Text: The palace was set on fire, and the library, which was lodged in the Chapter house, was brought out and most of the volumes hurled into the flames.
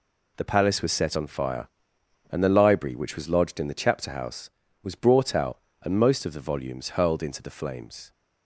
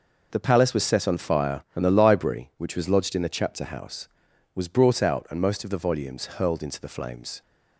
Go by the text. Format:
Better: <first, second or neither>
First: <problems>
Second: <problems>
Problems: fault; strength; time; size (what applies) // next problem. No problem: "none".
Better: neither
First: none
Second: none